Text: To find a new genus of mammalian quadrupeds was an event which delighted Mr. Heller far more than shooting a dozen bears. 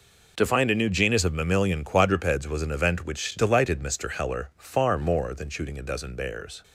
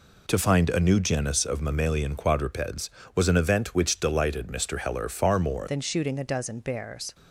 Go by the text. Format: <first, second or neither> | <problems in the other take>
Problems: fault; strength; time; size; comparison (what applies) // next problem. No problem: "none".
first | changes voice at "than"; from 5.6 s on; 1.5 s long